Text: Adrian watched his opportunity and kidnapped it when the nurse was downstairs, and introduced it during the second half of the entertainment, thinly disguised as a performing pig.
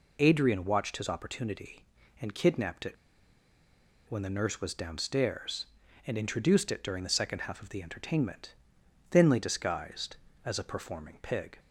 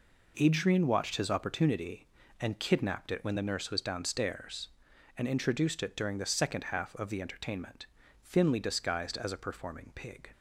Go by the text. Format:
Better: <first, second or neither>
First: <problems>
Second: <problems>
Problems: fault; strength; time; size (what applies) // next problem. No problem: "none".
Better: second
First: pauses between "it" and "when"; at 2.9 s; 1.1 s long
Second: none